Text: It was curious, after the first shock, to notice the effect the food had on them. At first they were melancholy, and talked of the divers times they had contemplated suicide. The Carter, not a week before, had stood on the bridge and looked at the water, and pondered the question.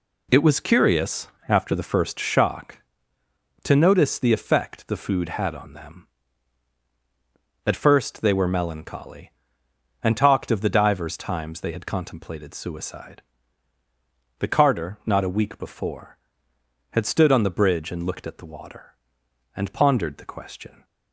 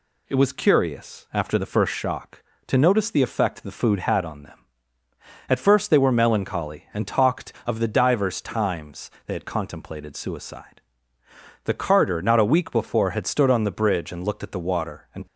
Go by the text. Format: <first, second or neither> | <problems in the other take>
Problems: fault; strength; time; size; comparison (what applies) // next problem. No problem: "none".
first | pauses between "times" and "they"; slight; at 9.1 s; 0.16 s long // stops before "pondered the question"; at 15.2 s